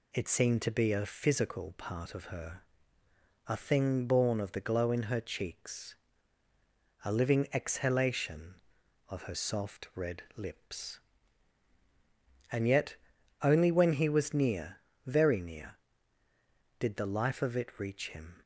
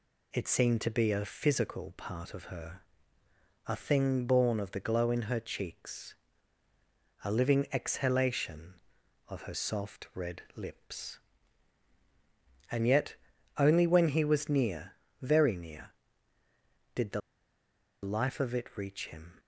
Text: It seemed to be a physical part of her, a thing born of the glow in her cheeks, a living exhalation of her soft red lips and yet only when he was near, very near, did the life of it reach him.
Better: first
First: pauses between "yet" and "only"; noticeable; at 12.9 s; 0.46 s long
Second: pauses between "yet" and "only"; at 13.1 s; 0.42 s long // pauses between "the" and "life"; noticeable; at 17.1 s; 0.83 s long

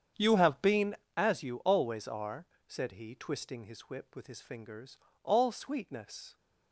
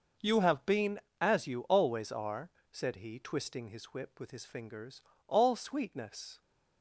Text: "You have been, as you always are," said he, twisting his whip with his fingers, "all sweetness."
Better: second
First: starts louder than the rest; strong; until 1.1 s; 8 dB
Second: none

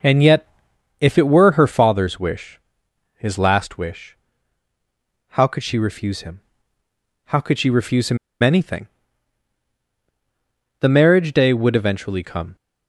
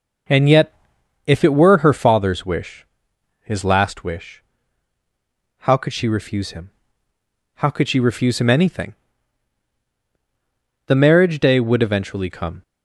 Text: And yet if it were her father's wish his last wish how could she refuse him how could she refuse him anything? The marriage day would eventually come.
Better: second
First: pauses between "yet" and "if"; noticeable; at 0.4 s; 0.54 s long // pauses between "wish" and "his"; noticeable; at 2.5 s; 0.58 s long // pauses between "wish" and "how"; at 4.1 s; 1.1 s long // pauses between "him" and "how"; noticeable; at 6.4 s; 0.86 s long // pauses between "him" and "anything"; slight; at 8.1 s; 0.25 s long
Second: pauses between "yet" and "if"; noticeable; at 0.7 s; 0.54 s long // pauses between "wish" and "his"; noticeable; at 2.8 s; 0.58 s long // pauses between "wish" and "how"; at 4.4 s; 1.1 s long // pauses between "him" and "how"; noticeable; at 6.6 s; 0.86 s long

